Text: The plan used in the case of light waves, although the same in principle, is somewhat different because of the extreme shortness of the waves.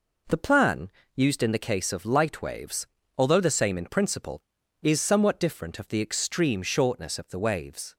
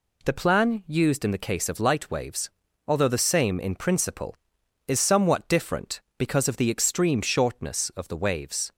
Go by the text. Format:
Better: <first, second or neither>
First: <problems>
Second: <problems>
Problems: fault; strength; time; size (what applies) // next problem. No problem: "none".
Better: second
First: pauses between "plan" and "used"; slight; at 0.8 s; 0.26 s long // skips "because"; at 5.7 s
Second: none